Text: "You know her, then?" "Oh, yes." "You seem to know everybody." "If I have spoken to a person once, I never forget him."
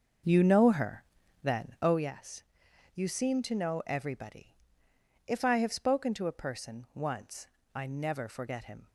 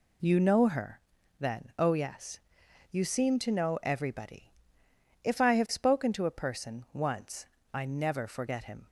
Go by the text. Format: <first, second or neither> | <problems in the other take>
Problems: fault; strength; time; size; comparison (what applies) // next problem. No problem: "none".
second | starts louder than the rest; until 2.0 s; 6.5 dB